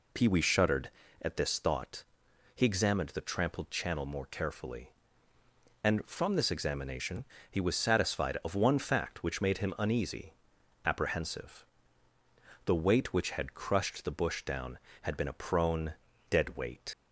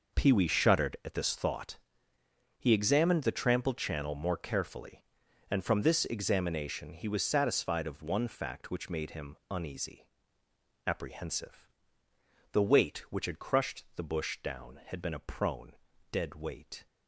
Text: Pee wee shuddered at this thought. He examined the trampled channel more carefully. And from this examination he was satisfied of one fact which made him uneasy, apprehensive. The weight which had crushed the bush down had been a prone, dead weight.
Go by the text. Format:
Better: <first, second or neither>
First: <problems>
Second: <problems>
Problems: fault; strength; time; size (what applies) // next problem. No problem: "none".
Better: second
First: pauses between "examination" and "he"; slight; at 7.2 s; 0.26 s long // leaves "weight" unfinished; at 16.9 s; 65 ms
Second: none